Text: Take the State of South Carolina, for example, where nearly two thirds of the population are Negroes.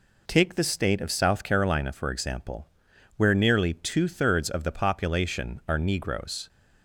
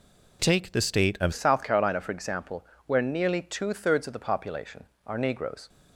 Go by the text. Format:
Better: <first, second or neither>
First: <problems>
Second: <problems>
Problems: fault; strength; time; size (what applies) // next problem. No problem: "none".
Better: first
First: none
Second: changes voice at "South"; from 1.3 s on; 4.3 s long